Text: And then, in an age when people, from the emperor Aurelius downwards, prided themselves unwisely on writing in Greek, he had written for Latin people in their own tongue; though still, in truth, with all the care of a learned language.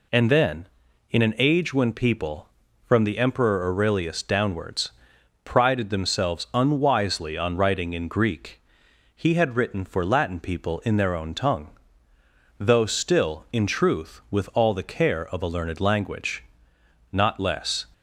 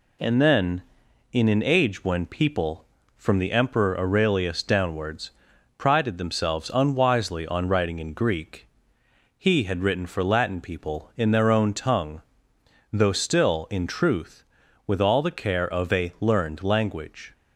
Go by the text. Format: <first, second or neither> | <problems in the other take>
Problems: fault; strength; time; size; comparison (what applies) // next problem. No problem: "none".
second | goes on to say "Not less"; noticeable; from 17.1 s on; 0.72 s long